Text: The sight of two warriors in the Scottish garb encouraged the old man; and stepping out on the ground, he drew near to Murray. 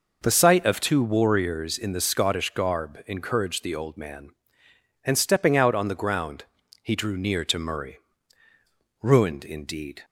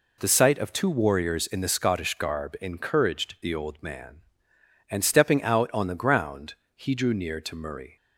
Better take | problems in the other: second | goes on to say "Ruined indeed"; noticeable; from 9.0 s on; 1.0 s long

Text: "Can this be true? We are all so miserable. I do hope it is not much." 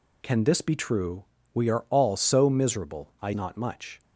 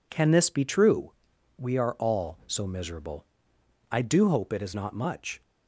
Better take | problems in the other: second | skips "do hope it is"; at 3.3 s

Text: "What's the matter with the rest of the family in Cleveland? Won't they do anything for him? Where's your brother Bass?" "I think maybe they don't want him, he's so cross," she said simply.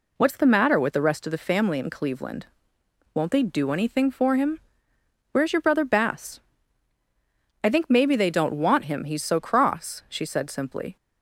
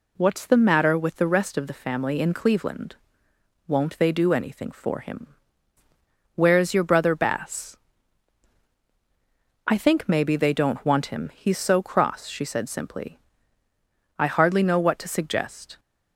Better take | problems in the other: first | goes on to say "I hardly know what to suggest"; from 14.1 s on; 1.6 s long

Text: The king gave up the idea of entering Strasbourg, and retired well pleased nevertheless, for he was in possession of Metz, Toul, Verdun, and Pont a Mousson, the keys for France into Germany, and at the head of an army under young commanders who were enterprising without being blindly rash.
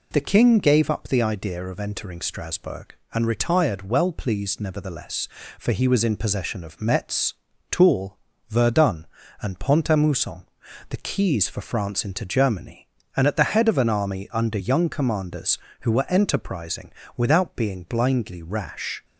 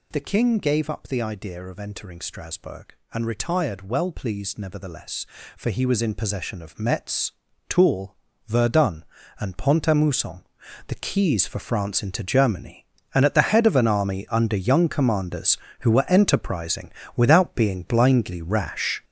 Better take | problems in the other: first | gets louder; strong; throughout; 7.5 dB // pauses between "enterprising" and "without"; slight; at 16.8 s; 0.24 s long; slight in the first

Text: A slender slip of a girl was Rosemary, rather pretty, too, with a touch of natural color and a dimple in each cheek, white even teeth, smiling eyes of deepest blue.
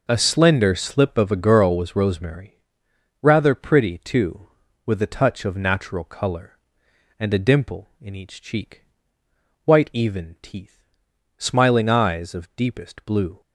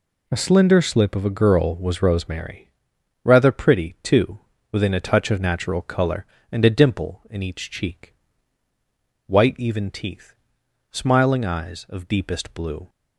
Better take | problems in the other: first | says "within" for "with"; at 4.7 s

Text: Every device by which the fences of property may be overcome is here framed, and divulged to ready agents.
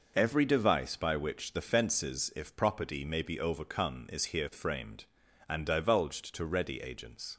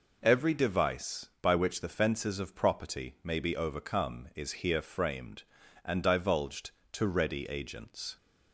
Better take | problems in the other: second | says "if" for "of"; at 2.3 s

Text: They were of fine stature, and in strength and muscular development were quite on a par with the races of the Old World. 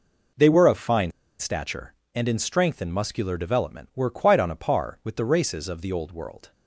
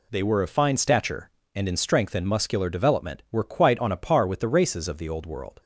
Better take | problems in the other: second | pauses between "fine" and "stature"; slight; at 1.1 s; 0.28 s long

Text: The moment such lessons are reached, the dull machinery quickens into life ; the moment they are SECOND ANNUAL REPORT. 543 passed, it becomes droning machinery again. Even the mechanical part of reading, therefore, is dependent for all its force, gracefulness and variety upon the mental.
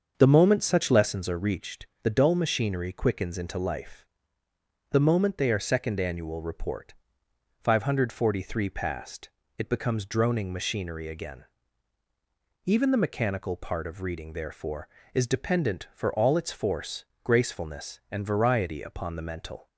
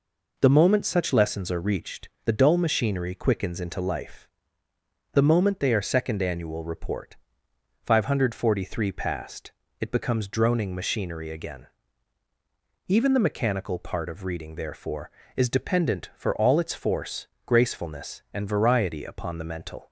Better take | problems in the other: second | starts louder than the rest; until 1.2 s; 7 dB

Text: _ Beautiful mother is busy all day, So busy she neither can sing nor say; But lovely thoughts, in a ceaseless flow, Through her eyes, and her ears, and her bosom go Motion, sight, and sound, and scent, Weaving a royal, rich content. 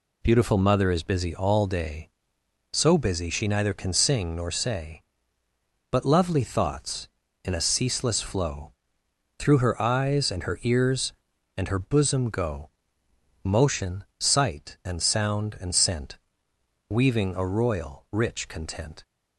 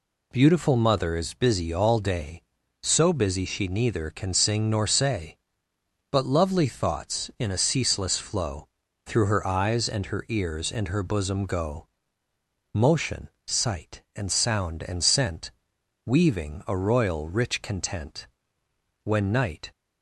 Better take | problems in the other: first | pauses between "go" and "Motion"; noticeable; at 11.8 s; 0.88 s long; noticeable in the first // goes on to say "When night"; noticeable; from 19.0 s on; 0.66 s long

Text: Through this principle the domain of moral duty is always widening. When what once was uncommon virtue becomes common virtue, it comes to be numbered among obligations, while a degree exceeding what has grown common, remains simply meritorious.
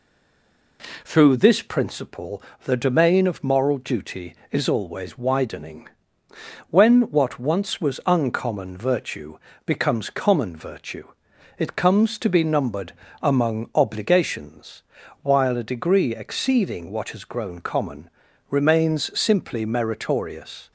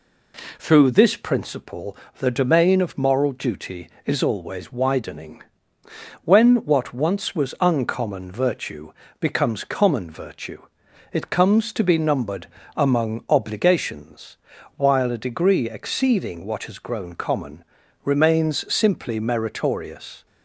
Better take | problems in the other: second | stays silent before the first word; slight; until 0.7 s; 0.7 s long // pauses between "principle" and "the"; slight; at 2.4 s; 0.22 s long; slight in the second // pauses between "virtue" and "becomes"; slight; at 9.3 s; 0.28 s long; slight in the second // pauses between "numbered" and "among"; slight; at 12.9 s; 0.28 s long; slight in the second

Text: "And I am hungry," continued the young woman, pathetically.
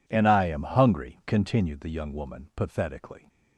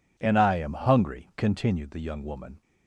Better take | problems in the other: first | stops before "pathetically"; at 2.6 s

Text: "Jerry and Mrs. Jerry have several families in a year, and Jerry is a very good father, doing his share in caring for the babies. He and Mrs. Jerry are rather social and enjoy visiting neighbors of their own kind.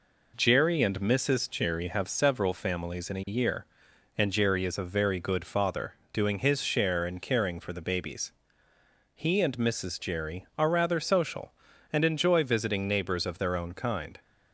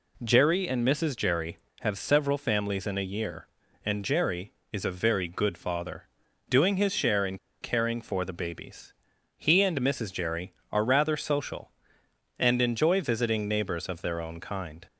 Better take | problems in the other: first | pauses between "in" and "caring"; slight; at 7.3 s; 0.25 s long

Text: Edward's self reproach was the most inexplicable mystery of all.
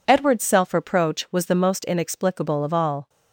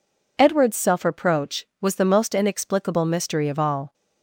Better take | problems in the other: second | skips "mystery"; at 2.6 s

